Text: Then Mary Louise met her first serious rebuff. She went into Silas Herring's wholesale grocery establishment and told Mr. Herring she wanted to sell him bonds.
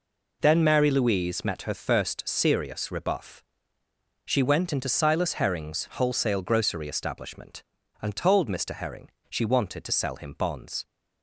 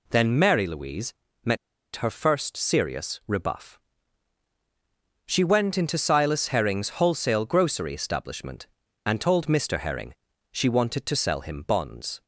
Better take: first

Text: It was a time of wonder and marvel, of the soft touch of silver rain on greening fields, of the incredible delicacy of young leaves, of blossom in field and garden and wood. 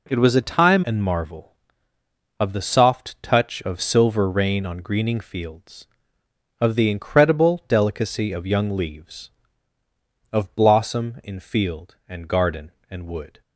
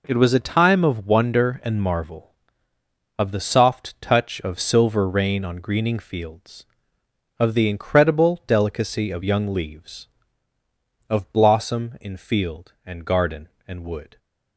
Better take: second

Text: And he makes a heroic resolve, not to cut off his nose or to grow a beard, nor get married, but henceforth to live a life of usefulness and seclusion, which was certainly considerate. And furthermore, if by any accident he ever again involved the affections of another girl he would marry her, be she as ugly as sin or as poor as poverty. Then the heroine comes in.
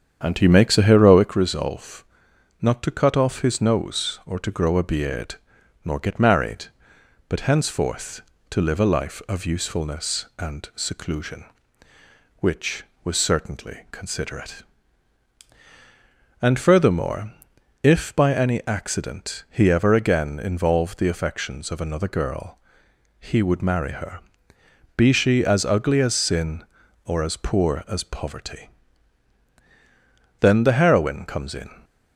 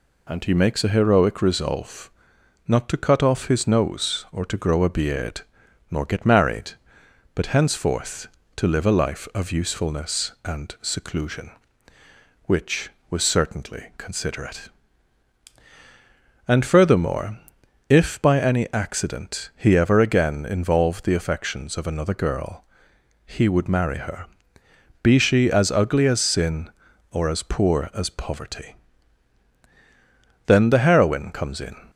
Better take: second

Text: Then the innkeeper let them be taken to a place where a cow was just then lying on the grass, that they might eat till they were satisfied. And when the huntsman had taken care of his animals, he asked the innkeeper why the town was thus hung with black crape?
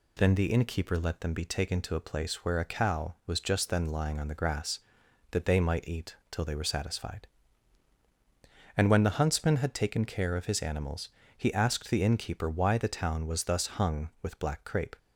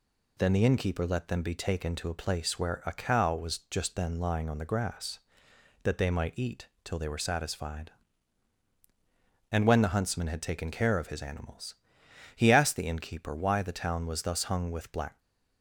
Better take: first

